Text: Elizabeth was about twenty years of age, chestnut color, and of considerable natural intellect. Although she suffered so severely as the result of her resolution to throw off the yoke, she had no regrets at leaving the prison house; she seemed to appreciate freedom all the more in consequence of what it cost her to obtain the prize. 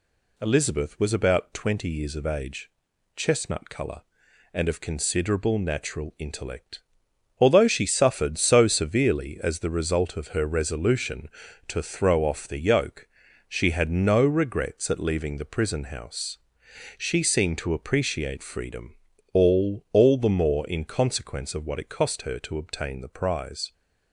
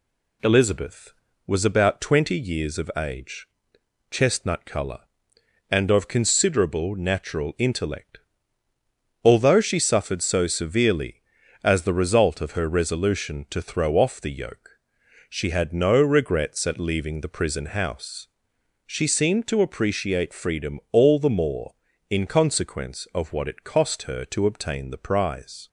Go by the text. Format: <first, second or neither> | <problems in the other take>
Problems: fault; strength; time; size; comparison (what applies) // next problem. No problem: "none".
second | pauses between "freedom" and "all"; at 18.9 s; 0.38 s long // says "all" twice; at 19.9 s